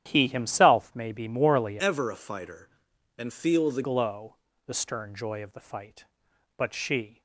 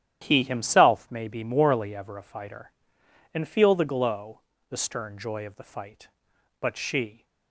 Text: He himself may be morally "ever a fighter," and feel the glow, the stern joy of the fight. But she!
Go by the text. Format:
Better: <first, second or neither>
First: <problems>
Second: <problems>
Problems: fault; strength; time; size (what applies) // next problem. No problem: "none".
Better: second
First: starts louder than the rest; strong; until 1.0 s; 10.5 dB // changes voice from "ever" to "the"; from 1.7 to 3.8 s; 2.1 s long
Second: starts louder than the rest; strong; until 1.2 s; 11 dB